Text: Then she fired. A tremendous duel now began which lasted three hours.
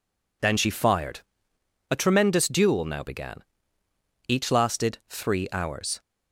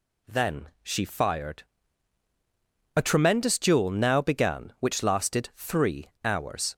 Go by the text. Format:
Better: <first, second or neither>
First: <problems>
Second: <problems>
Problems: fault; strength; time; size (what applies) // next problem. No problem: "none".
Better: second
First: says "each" for "which"; at 4.2 s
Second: none